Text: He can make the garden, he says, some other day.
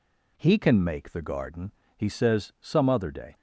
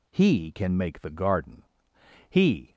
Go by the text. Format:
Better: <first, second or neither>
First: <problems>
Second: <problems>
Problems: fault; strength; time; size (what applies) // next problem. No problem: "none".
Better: first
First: none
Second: stops before "says some other day"; at 2.7 s